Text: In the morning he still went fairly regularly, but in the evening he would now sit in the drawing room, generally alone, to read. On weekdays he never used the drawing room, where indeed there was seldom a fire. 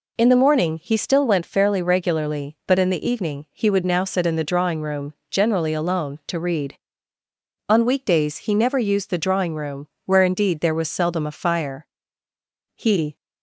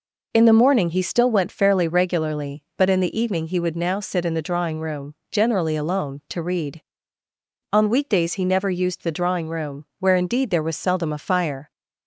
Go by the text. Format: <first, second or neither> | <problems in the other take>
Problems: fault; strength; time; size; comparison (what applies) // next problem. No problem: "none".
second | goes on to say "He"; slight; from 12.7 s on; 0.40 s long